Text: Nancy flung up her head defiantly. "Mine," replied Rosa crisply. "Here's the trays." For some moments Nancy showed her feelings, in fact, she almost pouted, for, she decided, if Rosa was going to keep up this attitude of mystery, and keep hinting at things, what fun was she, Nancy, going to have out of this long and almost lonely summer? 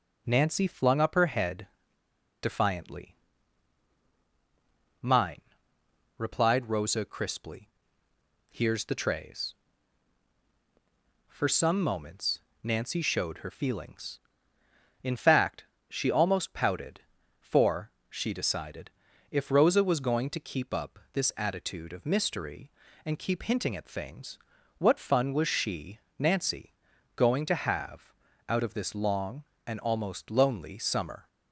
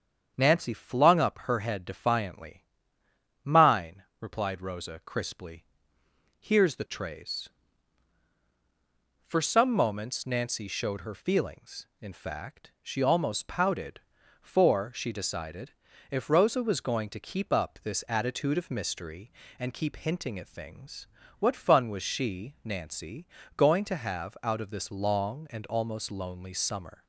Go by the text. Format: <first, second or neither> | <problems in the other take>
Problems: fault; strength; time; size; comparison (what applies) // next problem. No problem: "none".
second | starts louder than the rest; until 1.2 s; 6.5 dB; strong in the second // pauses between "head" and "defiantly"; noticeable; at 1.6 s; 0.74 s long // pauses between "moments" and "Nancy"; slight; at 12.4 s; 0.22 s long // pauses between "have" and "out"; at 28.1 s; 0.38 s long